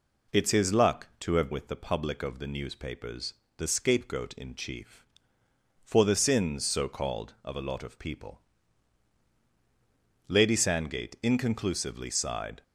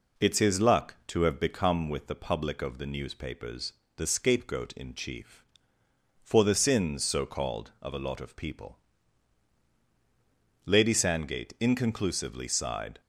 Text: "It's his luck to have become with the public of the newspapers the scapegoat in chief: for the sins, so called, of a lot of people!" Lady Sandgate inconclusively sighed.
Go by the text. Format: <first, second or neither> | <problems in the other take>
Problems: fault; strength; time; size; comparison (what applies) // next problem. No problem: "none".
second | skips "become"; at 1.5 s // pauses between "newspapers" and "the"; slight; at 3.3 s; 0.24 s long; slight in the second